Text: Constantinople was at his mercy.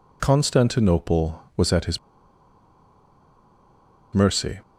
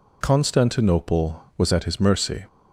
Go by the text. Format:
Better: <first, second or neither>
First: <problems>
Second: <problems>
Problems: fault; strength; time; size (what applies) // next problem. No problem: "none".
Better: second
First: pauses between "his" and "mercy"; strong; at 1.9 s; 2.1 s long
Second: none